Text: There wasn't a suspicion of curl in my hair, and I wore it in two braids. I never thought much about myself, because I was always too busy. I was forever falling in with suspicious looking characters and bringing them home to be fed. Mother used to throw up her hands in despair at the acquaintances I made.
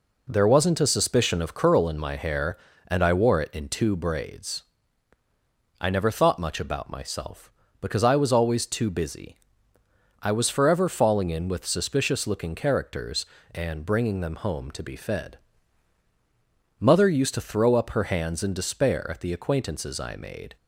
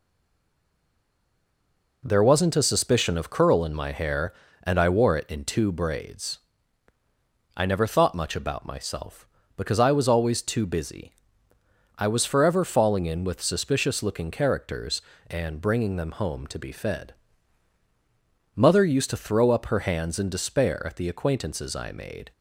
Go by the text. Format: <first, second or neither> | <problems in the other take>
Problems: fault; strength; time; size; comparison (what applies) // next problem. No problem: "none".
first | stays silent before the first word; noticeable; until 2.0 s; 2.0 s long